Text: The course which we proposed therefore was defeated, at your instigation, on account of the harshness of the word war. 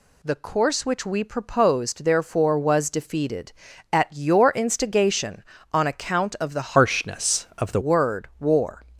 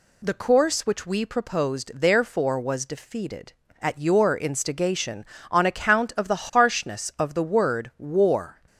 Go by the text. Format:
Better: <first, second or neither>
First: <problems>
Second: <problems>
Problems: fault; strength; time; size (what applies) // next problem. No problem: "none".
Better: second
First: changes voice from "harshness" to "the"; from 6.7 to 7.7 s; 1.0 s long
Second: none